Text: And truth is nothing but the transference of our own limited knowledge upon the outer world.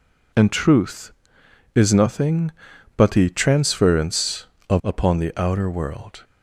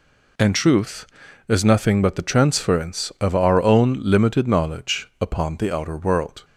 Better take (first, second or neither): second